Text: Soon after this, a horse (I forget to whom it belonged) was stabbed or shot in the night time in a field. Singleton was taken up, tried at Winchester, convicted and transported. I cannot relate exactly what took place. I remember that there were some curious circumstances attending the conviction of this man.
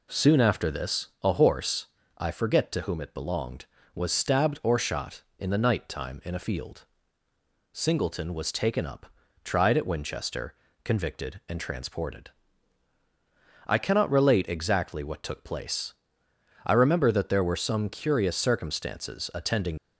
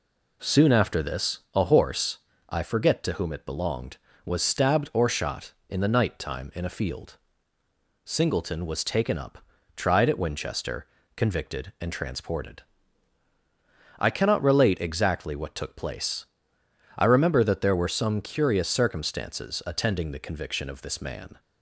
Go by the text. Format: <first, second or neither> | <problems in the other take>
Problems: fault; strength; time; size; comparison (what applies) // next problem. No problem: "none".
second | stops before "the conviction of this man"; at 19.7 s